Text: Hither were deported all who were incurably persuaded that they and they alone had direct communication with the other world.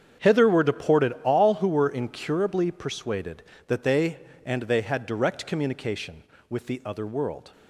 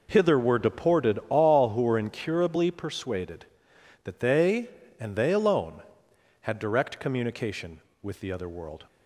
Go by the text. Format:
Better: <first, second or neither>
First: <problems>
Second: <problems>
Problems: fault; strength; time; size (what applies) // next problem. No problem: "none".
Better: second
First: starts louder than the rest; strong; until 1.3 s; 8 dB // skips "alone"; at 4.8 s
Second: none